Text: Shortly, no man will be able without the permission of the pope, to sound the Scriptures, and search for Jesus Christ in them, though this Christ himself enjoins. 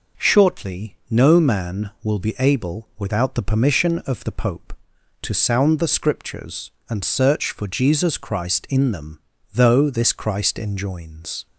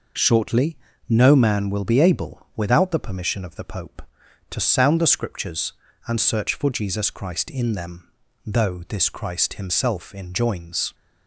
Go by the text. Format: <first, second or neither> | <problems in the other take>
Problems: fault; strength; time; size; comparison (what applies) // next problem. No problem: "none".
second | skips "himself"; at 10.5 s